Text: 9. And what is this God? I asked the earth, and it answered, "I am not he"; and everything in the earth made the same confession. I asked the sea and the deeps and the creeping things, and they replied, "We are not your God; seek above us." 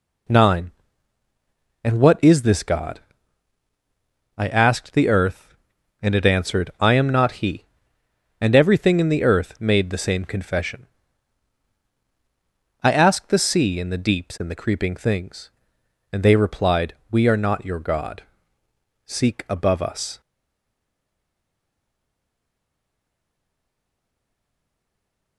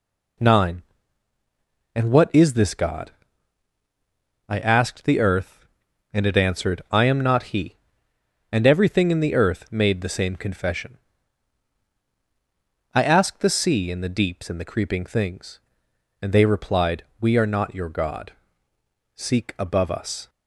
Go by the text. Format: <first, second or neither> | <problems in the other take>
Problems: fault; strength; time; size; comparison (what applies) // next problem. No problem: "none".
second | stays silent after the last word; strong; from 20.2 s on; 5.1 s long